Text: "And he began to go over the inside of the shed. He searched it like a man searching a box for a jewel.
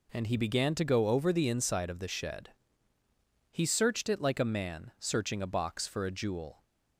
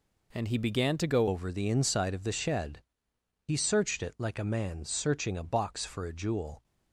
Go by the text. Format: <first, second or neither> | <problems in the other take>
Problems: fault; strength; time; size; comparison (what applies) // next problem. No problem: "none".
first | changes voice at "over"; from 1.2 s on; 5.4 s long